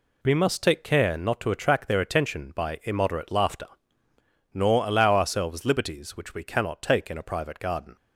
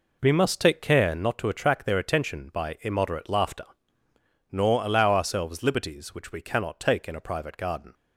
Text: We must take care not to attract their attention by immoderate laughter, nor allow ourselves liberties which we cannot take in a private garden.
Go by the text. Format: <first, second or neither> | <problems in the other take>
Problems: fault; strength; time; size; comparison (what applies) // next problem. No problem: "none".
first | starts louder than the rest; until 1.3 s; 3.5 dB